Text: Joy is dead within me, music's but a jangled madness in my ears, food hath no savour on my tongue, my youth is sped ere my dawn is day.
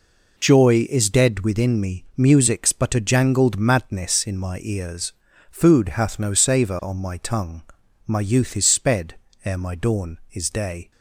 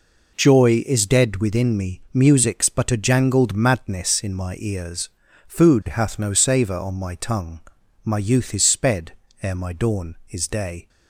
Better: neither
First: pauses between "sped" and "ere"; slight; at 9.1 s; 0.30 s long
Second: pauses between "sped" and "ere"; slight; at 9.1 s; 0.30 s long

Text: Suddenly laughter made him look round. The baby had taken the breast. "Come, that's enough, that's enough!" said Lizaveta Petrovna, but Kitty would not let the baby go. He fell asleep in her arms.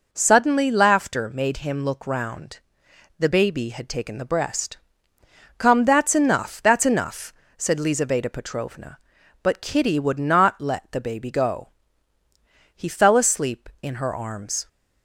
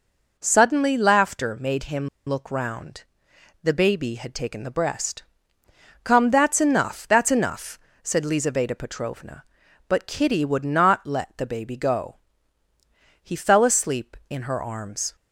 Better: first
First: none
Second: pauses between "him" and "look"; slight; at 2.0 s; 0.20 s long

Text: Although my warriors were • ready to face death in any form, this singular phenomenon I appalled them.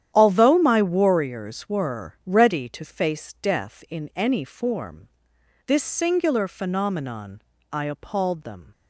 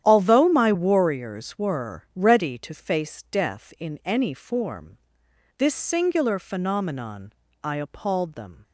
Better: neither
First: starts louder than the rest; strong; until 1.1 s; 10 dB // pauses between "phenomenon" and "I"; slight; at 7.4 s; 0.30 s long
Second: starts louder than the rest; strong; until 1.0 s; 10 dB // pauses between "phenomenon" and "I"; slight; at 7.3 s; 0.30 s long

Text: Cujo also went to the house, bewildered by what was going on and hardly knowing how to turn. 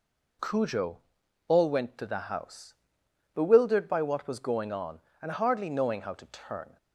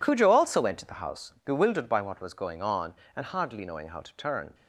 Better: second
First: says "all" for "also"; at 1.4 s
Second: none

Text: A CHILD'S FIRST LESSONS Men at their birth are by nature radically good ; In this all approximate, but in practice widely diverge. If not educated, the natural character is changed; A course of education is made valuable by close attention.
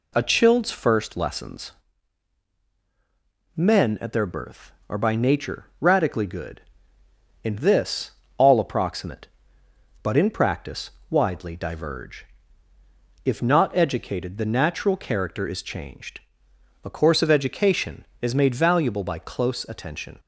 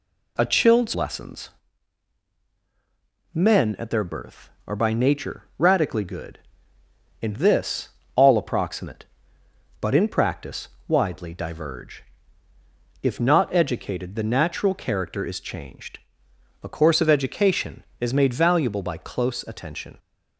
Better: first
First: pauses between "LESSONS" and "Men"; strong; at 1.7 s; 1.8 s long // pauses between "this" and "all"; slight; at 8.1 s; 0.26 s long // pauses between "practice" and "widely"; slight; at 10.9 s; 0.18 s long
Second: skips "FIRST"; at 0.9 s // pauses between "LESSONS" and "Men"; strong; at 1.4 s; 1.8 s long // pauses between "this" and "all"; slight; at 7.8 s; 0.26 s long // pauses between "practice" and "widely"; slight; at 10.6 s; 0.18 s long

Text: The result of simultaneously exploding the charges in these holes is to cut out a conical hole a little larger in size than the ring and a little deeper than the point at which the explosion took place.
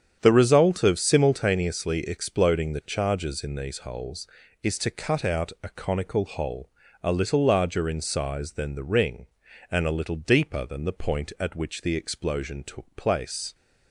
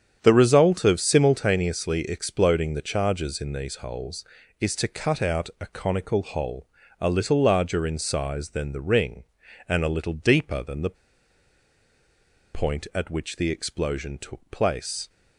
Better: first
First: starts louder than the rest; strong; until 1.2 s; 8 dB // pauses between "hole" and "a"; slight; at 6.6 s; 0.34 s long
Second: starts louder than the rest; strong; until 1.2 s; 8 dB // pauses between "hole" and "a"; slight; at 6.6 s; 0.34 s long // pauses between "the" and "point"; strong; at 10.9 s; 1.5 s long

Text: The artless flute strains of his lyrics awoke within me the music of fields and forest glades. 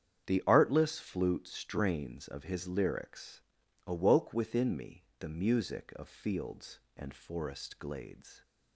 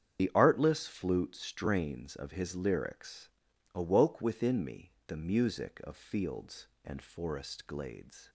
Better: first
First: starts louder than the rest; strong; until 1.3 s; 8.5 dB // pauses between "lyrics" and "awoke"; noticeable; at 3.4 s; 0.46 s long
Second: loses the start of "The"; at 0.1 s; 45 ms // starts louder than the rest; strong; until 1.2 s; 8.5 dB // pauses between "lyrics" and "awoke"; noticeable; at 3.2 s; 0.46 s long

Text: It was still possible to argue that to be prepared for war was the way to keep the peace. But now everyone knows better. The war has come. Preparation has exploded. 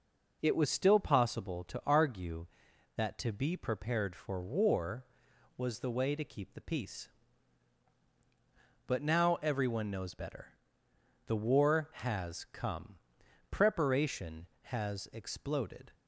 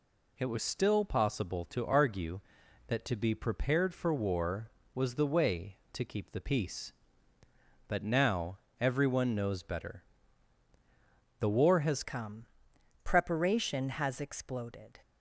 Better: first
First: none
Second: pauses between "now" and "everyone"; slight; at 8.5 s; 0.22 s long // changes voice at "come"; from 12.0 s on; 2.9 s long

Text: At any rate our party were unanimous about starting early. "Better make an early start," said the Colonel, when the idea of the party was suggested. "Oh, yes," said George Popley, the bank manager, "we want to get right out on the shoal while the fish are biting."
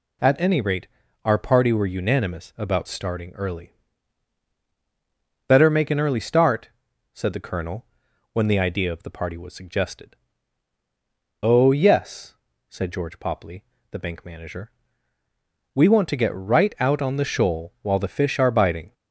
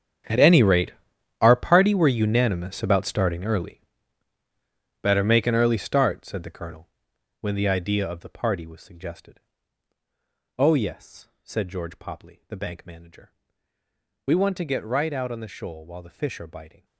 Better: first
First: pauses between "rate" and "our"; at 0.8 s; 0.38 s long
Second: gets quieter; strong; throughout; 17 dB // pauses between "rate" and "our"; noticeable; at 0.9 s; 0.50 s long

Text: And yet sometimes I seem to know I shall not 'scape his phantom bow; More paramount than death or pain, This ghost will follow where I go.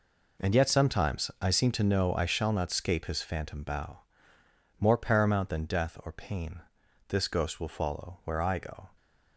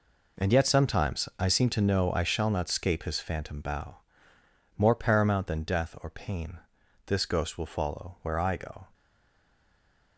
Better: first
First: none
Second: stays silent after the last word; noticeable; from 8.9 s on; 1.2 s long

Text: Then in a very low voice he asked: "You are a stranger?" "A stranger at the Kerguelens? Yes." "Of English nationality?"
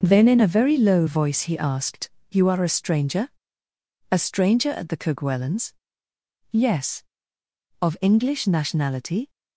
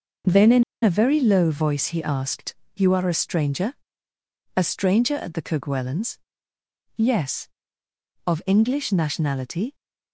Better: first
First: none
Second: pauses between "in" and "a"; slight; at 0.6 s; 0.19 s long

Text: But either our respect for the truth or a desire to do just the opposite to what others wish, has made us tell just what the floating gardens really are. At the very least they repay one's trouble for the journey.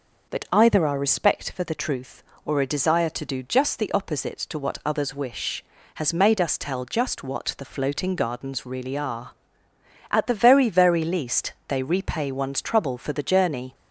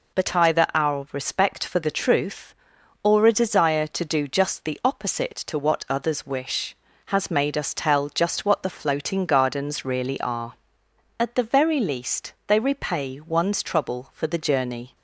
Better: second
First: says "very" twice; at 10.6 s // pauses between "least" and "they"; slight; at 11.5 s; 0.16 s long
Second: none

